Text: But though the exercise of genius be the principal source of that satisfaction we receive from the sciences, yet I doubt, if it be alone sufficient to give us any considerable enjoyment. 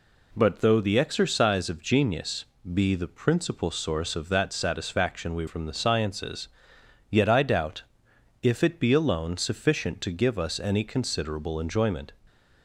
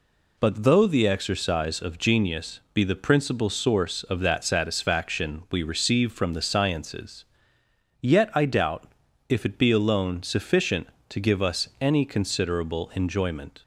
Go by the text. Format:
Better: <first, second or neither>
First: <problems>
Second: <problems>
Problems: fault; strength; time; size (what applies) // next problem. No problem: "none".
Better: second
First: pauses between "genius" and "be"; slight; at 2.4 s; 0.28 s long // skips "receive"; at 5.4 s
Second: none